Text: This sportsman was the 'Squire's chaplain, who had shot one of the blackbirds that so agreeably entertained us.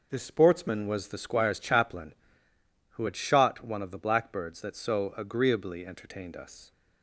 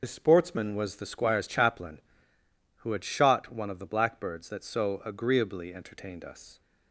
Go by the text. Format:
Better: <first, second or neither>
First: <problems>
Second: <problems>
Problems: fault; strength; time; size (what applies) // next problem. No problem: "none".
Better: first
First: none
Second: loses the start of "This"; at 0.0 s; 35 ms